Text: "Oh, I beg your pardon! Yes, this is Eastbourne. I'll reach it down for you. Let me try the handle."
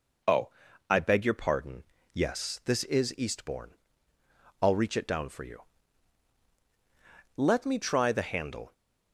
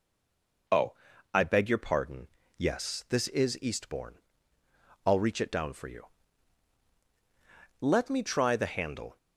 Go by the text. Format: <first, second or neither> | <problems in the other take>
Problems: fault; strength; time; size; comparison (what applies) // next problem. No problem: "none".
first | stays silent before the first word; slight; until 0.6 s; 0.6 s long